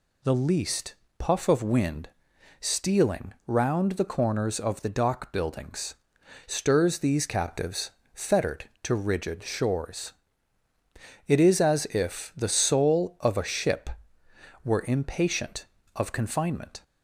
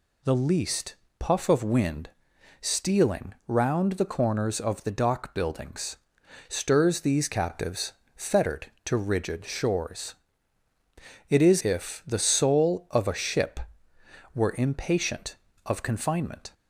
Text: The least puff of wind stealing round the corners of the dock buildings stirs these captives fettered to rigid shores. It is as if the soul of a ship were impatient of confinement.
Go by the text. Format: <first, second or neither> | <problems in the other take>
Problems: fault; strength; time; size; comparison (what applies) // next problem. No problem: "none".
first | pauses between "least" and "puff"; slight; at 0.9 s; 0.24 s long; slight in the first // pauses between "wind" and "stealing"; noticeable; at 2.1 s; 0.50 s long; noticeable in the first // pauses between "buildings" and "stirs"; noticeable; at 5.9 s; 0.50 s long; noticeable in the first // pauses between "captives" and "fettered"; slight; at 7.9 s; 0.22 s long; slight in the first // skips "as"; at 11.6 s